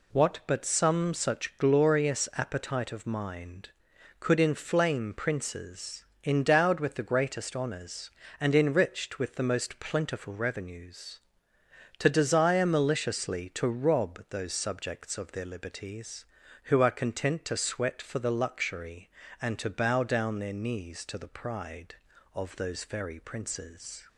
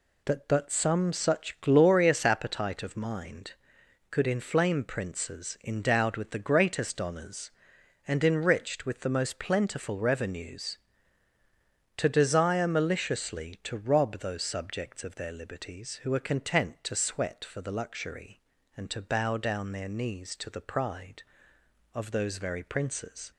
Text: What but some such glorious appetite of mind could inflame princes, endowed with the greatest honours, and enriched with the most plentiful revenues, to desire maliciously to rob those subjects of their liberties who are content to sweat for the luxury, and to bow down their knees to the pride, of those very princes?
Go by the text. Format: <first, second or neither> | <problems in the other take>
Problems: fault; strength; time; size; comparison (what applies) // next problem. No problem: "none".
first | says "That" for "What"; at 0.2 s